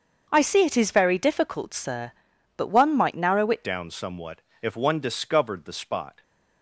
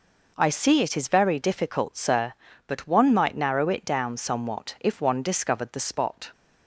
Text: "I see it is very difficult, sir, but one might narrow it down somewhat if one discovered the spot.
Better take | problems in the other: second | starts louder than the rest; until 1.3 s; 6.5 dB // changes voice at "down"; from 3.6 s on; 2.6 s long // pauses between "somewhat" and "if"; slight; at 4.4 s; 0.22 s long

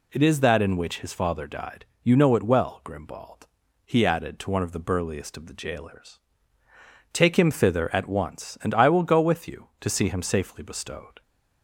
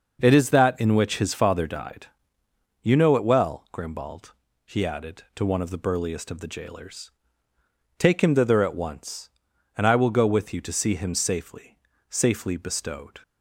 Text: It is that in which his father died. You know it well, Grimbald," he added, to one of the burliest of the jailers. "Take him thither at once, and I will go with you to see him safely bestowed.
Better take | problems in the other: first | says "safely" twice; at 12.0 s

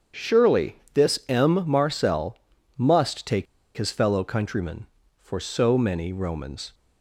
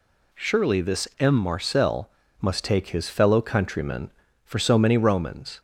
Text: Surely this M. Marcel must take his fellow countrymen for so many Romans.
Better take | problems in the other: second | starts louder than the rest; strong; until 1.4 s; 7.5 dB // pauses between "Surely" and "this"; slight; at 0.7 s; 0.16 s long // pauses between "Marcel" and "must"; at 2.3 s; 0.38 s long; slight in the second // pauses between "take" and "his"; slight; at 3.4 s; 0.32 s long

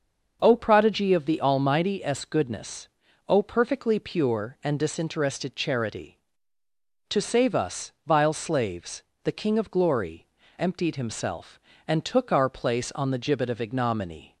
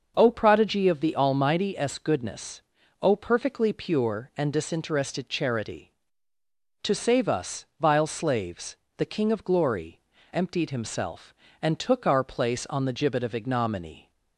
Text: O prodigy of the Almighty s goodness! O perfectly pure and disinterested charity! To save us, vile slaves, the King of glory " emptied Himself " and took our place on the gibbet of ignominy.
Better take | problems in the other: neither | starts louder than the rest; the same in both

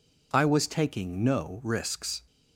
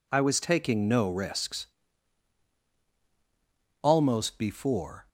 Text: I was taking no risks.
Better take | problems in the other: first | goes on to say "Almost before"; noticeable; from 3.8 s on; 1.2 s long

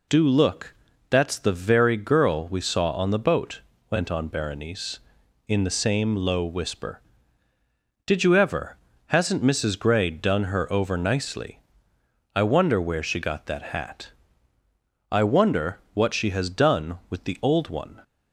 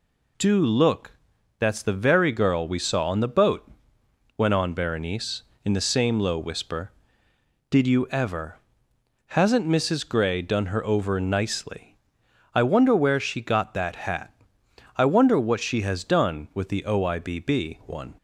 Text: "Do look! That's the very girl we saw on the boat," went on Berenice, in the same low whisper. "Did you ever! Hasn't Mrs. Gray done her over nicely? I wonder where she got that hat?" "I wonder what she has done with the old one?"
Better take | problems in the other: first | says "oibb" for "old"; at 16.8 s

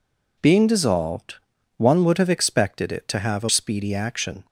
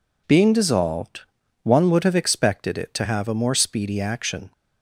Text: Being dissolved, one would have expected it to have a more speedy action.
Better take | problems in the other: second | skips "more"; at 3.4 s

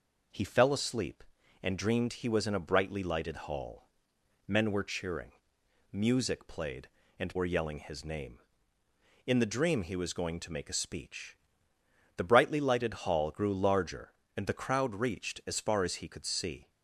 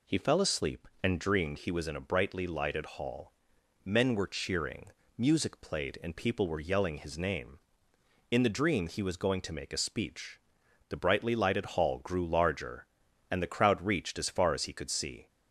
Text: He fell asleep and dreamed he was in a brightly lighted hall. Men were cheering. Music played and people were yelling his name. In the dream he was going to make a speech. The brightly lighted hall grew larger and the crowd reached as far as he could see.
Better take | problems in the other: second | skips "people"; at 7.3 s

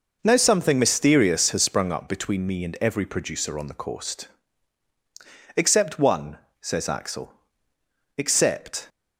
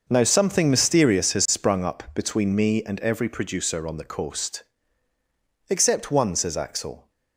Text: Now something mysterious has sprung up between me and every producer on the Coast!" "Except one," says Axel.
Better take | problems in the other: second | goes on to say "Except"; noticeable; from 8.1 s on; 0.72 s long

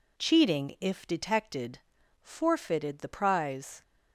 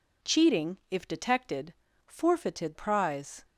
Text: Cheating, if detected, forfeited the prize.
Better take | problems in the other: first | skips "the"; at 2.7 s

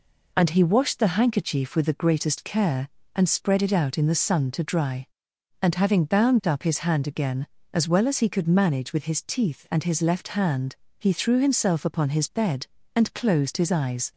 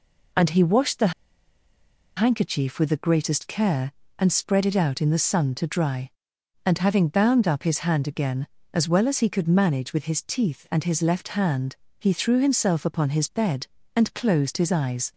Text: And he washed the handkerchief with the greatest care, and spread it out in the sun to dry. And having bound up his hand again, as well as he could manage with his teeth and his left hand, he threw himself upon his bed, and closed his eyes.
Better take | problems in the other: first | pauses between "the" and "handkerchief"; at 1.1 s; 1.0 s long

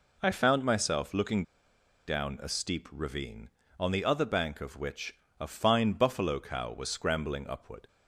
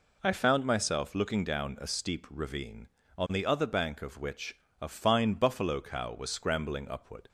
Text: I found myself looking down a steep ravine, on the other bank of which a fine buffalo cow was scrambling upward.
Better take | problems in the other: second | pauses between "looking" and "down"; noticeable; at 1.4 s; 0.63 s long // pauses between "which" and "a"; slight; at 5.1 s; 0.26 s long; slight in the second

